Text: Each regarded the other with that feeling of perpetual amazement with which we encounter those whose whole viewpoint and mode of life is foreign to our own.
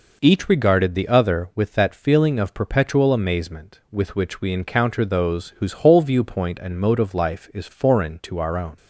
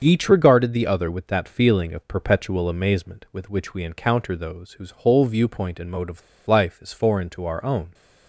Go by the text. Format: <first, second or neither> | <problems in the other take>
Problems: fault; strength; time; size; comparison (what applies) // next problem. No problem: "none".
first | starts louder than the rest; until 1.0 s; 7 dB // pauses between "of" and "life"; slight; at 6.2 s; 0.27 s long